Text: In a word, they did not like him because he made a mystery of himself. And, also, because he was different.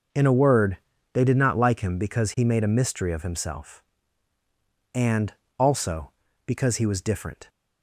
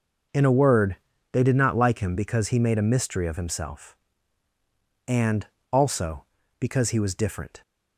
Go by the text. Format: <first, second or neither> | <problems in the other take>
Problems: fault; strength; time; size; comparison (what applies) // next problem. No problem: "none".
neither | none